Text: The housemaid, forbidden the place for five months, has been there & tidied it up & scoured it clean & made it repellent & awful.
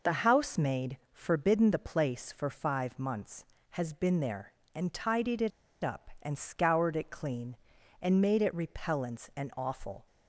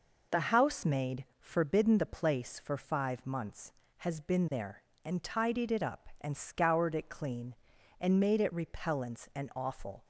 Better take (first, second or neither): second